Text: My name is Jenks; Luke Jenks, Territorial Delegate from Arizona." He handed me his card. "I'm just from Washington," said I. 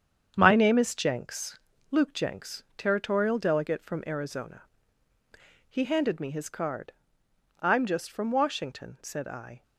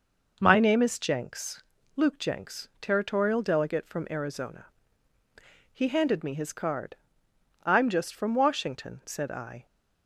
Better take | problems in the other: second | gets quieter; strong; throughout; 8 dB

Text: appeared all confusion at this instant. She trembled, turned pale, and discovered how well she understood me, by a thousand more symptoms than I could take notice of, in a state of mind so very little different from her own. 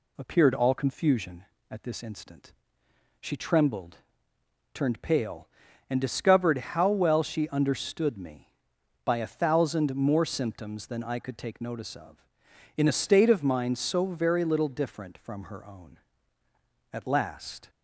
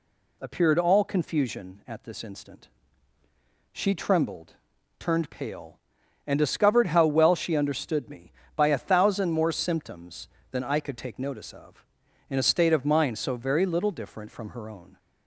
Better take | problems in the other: second | goes on to say "At last"; noticeable; from 16.9 s on; 0.78 s long

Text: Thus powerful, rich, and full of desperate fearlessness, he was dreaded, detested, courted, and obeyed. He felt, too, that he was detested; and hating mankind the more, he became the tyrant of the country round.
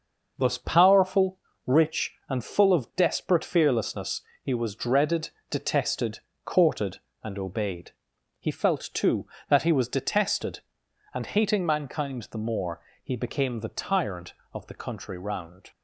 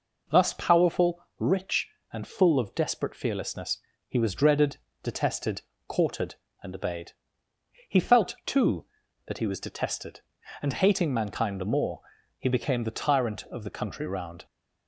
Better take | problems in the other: second | gets quieter; noticeable; throughout; 5.5 dB

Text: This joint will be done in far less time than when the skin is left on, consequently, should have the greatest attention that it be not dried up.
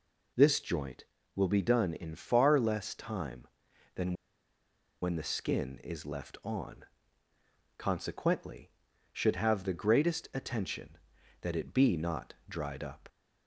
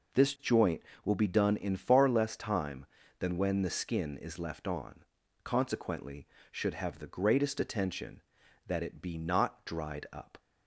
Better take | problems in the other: second | pauses between "than" and "when"; noticeable; at 4.1 s; 0.88 s long

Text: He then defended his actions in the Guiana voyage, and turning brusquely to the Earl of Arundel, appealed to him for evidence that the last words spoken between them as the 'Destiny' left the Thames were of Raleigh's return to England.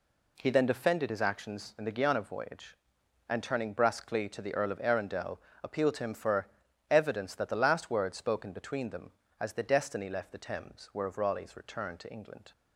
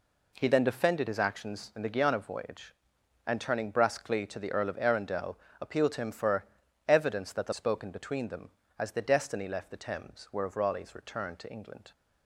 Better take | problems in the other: first | pauses between "for" and "evidence"; at 6.4 s; 0.44 s long; also in the first // skips "last words"; at 7.5 s

